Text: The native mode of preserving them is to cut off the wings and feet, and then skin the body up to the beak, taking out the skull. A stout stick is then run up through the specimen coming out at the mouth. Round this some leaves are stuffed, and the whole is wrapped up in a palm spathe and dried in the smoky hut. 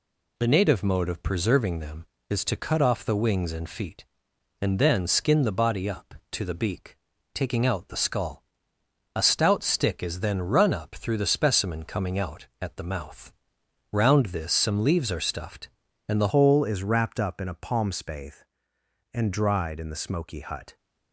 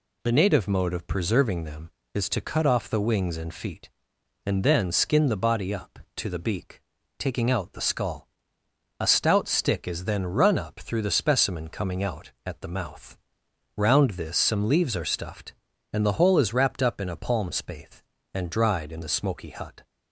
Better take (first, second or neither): second